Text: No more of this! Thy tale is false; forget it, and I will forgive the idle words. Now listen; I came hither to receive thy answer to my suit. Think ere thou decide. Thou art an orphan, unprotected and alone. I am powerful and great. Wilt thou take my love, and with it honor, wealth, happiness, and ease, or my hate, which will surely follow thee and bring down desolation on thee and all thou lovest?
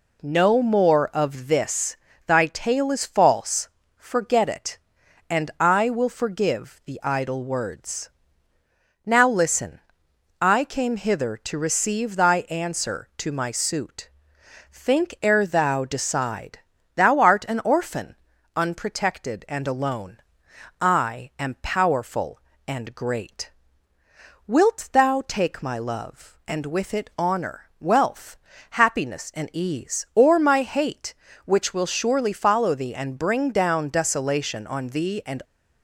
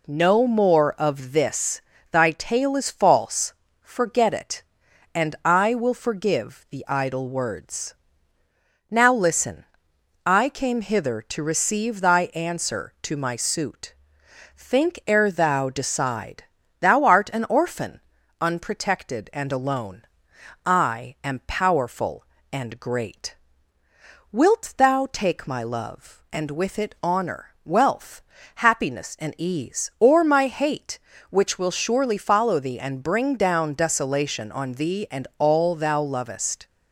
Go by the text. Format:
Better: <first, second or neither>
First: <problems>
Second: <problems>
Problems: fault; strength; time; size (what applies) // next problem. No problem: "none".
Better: second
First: stops before "all thou lovest"; at 35.4 s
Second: none